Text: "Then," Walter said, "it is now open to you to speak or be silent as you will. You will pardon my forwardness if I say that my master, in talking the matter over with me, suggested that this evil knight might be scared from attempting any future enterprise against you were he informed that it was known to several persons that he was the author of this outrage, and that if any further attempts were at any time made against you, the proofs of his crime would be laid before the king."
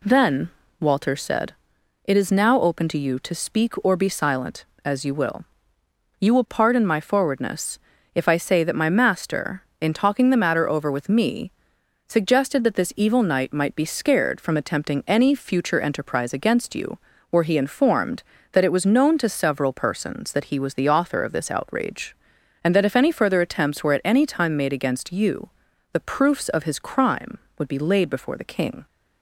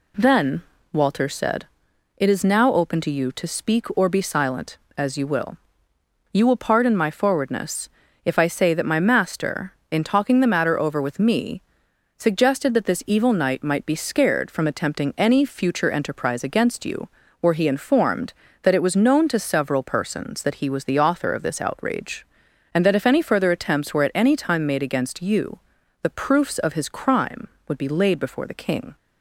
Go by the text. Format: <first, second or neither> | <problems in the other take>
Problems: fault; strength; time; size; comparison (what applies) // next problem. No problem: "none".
neither | pauses between "forwardness" and "if"; slight; the same in both